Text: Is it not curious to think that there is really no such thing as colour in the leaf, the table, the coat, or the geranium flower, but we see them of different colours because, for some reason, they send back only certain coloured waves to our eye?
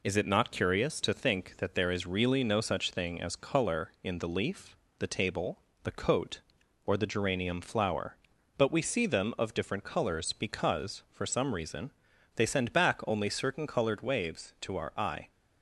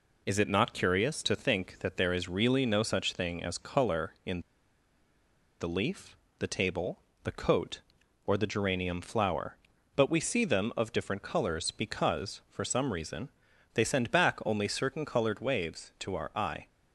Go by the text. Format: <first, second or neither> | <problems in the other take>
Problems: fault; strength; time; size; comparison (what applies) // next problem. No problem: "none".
first | pauses between "in" and "the"; at 4.4 s; 1.1 s long